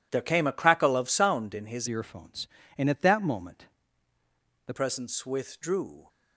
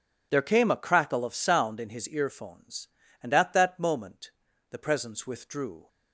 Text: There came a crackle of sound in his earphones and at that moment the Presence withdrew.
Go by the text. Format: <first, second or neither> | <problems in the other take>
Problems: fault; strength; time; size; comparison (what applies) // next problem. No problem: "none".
second | changes voice from "earphones" to "the"; from 1.8 to 4.7 s; 2.9 s long // pauses between "moment" and "the"; at 3.6 s; 1.0 s long; also in the second